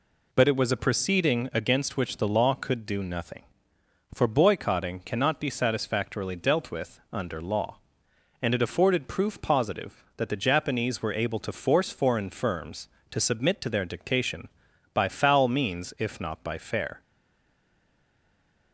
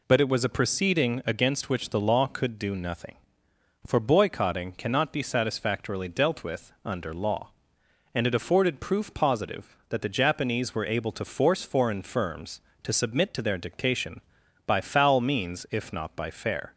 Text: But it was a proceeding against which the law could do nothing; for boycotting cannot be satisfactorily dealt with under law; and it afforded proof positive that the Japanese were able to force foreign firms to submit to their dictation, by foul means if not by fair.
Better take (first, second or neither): second